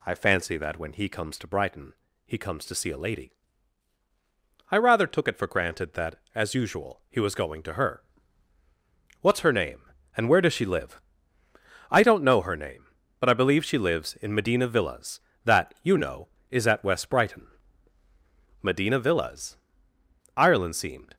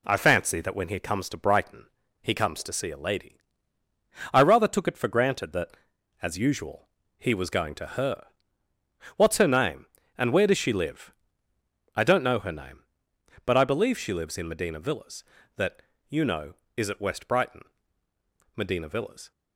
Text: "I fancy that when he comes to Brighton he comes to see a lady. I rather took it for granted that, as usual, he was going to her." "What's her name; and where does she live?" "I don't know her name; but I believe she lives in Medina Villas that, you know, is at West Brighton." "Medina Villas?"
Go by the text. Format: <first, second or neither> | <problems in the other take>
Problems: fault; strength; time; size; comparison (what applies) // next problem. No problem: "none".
second | pauses between "Brighton" and "he"; slight; at 1.9 s; 0.32 s long; slight in the second // goes on to say "Ireland seemed"; noticeable; from 20.3 s on; 0.80 s long